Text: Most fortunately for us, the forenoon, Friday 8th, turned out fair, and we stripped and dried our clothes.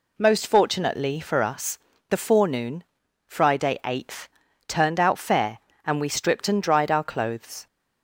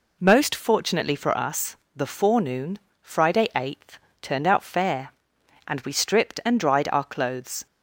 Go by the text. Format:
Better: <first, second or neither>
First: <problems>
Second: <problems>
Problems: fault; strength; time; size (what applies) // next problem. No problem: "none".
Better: neither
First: none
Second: none